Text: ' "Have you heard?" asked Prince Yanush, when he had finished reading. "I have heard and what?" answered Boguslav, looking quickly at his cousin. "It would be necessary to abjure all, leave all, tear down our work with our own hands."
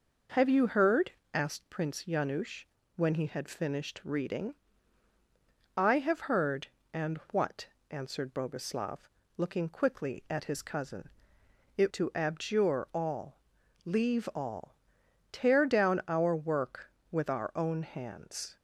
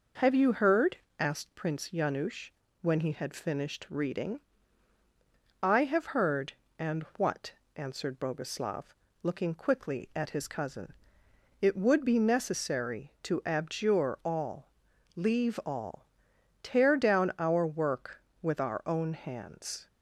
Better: second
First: pauses between "and" and "what"; slight; at 7.1 s; 0.16 s long // skips "would be necessary"; at 11.9 s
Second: pauses between "and" and "what"; slight; at 7.0 s; 0.16 s long

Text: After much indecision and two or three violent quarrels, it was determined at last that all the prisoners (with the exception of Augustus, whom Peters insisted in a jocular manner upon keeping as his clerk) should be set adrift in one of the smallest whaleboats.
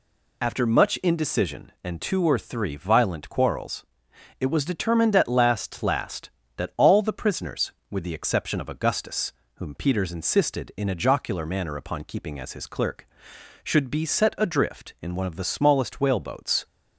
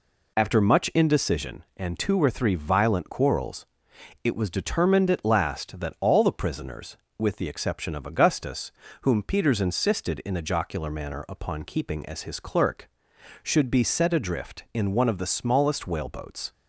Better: second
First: says "last" twice; at 5.8 s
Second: none

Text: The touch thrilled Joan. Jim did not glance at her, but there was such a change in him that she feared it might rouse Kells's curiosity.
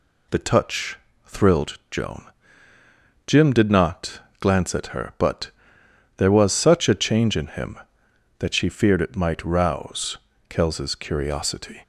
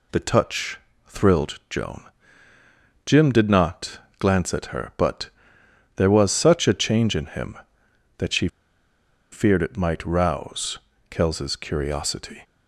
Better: first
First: pauses between "touch" and "thrilled"; slight; at 0.9 s; 0.28 s long // pauses between "not" and "glance"; slight; at 4.2 s; 0.18 s long // pauses between "but" and "there"; noticeable; at 5.5 s; 0.68 s long // pauses between "rouse" and "Kells's"; slight; at 10.1 s; 0.30 s long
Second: pauses between "touch" and "thrilled"; slight; at 0.7 s; 0.28 s long // pauses between "not" and "glance"; slight; at 3.9 s; 0.18 s long // pauses between "but" and "there"; noticeable; at 5.2 s; 0.68 s long // pauses between "she" and "feared"; noticeable; at 8.4 s; 0.84 s long // pauses between "rouse" and "Kells's"; slight; at 10.7 s; 0.30 s long

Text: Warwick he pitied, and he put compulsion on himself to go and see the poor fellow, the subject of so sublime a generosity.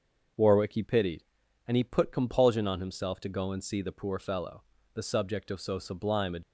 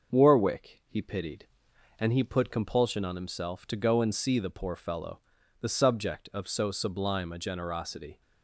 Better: second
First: starts louder than the rest; until 1.8 s; 6.5 dB // stops before "generosity"; at 6.4 s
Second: starts louder than the rest; until 1.2 s; 6 dB

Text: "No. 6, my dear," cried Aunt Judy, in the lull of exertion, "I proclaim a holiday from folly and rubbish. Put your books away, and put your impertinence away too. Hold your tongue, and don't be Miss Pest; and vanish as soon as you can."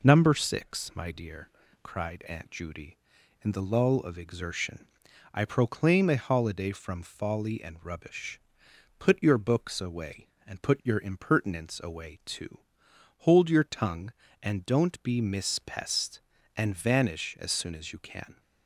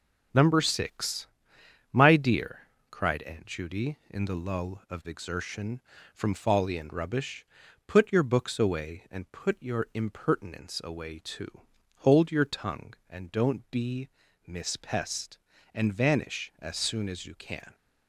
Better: first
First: none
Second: skips "I proclaim a holiday"; at 5.9 s // pauses between "be" and "Miss"; at 14.0 s; 0.38 s long

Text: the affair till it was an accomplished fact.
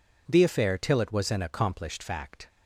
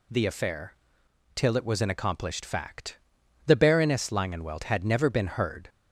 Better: first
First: none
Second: pauses between "affair" and "till"; noticeable; at 0.7 s; 0.60 s long // goes on to say "The Baroness Langenwelt had never been heard"; strong; from 3.4 s on; 2.2 s long

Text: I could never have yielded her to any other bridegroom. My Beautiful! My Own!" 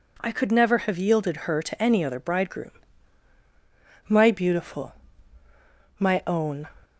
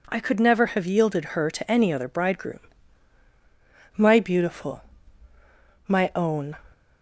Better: neither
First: none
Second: none

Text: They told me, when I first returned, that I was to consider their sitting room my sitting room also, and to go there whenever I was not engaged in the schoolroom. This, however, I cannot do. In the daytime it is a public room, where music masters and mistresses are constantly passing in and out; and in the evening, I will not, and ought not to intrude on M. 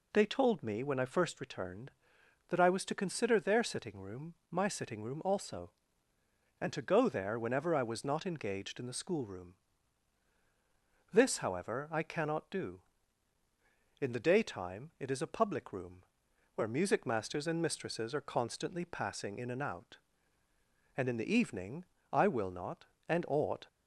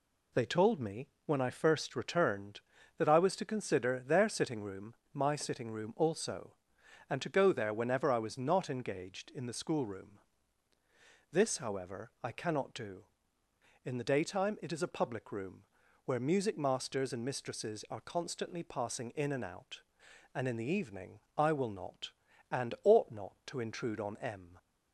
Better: second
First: pauses between "room" and "my"; slight; at 4.3 s; 0.16 s long // stops before "not to intrude on M"; at 23.6 s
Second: pauses between "room" and "my"; slight; at 4.9 s; 0.20 s long

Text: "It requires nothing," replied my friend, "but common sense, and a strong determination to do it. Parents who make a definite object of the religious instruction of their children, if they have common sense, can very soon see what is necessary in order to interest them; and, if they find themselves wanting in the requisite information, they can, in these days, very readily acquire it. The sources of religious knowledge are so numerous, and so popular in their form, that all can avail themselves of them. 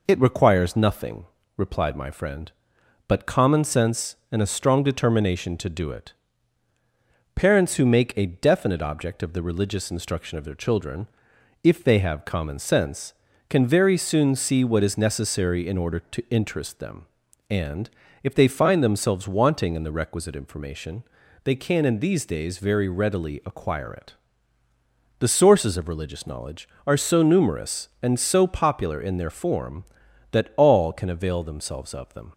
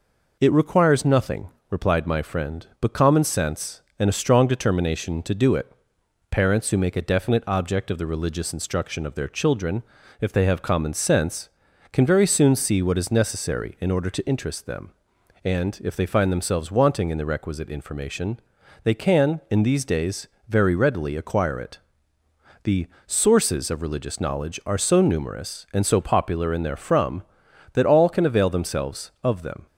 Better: first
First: none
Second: pauses between "The" and "sources"; slight; at 22.8 s; 0.22 s long // says "from" for "form"; at 26.7 s

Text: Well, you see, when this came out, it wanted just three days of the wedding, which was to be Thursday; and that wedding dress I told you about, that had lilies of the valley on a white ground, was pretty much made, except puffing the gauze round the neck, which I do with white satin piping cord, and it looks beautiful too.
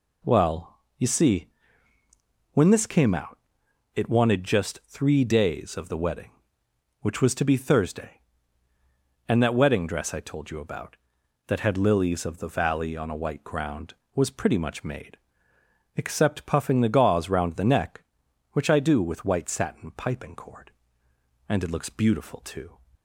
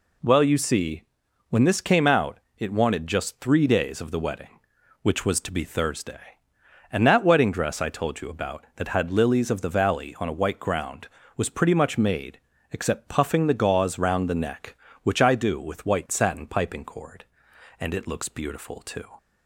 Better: neither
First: none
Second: none

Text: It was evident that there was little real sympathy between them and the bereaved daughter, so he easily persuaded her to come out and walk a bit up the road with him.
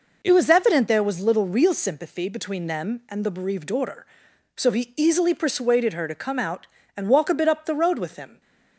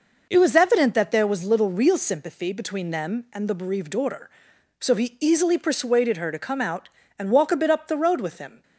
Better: second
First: skips "that"; at 0.8 s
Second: none

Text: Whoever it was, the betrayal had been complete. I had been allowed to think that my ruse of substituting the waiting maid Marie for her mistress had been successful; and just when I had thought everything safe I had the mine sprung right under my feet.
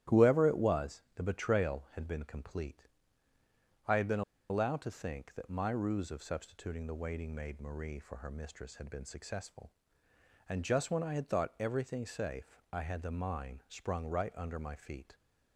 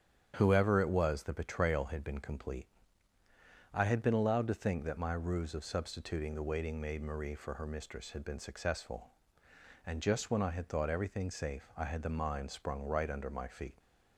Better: second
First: starts louder than the rest; strong; until 1.2 s; 12.5 dB // pauses between "been" and "allowed"; slight; at 4.2 s; 0.26 s long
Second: starts louder than the rest; strong; until 1.3 s; 9 dB

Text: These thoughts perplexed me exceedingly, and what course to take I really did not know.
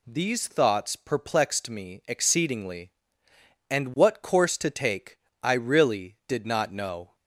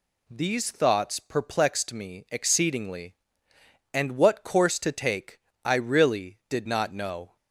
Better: neither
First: pauses between "take" and "I"; slight; at 5.1 s; 0.26 s long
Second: pauses between "take" and "I"; slight; at 5.3 s; 0.26 s long

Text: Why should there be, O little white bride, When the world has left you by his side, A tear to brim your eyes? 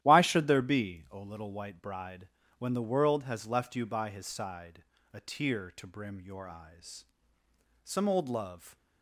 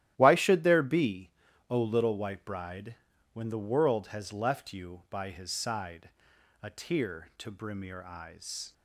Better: second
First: starts louder than the rest; strong; until 1.0 s; 12.5 dB // goes on to say "Some old love"; noticeable; from 7.8 s on; 0.92 s long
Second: starts louder than the rest; strong; until 1.1 s; 13.5 dB

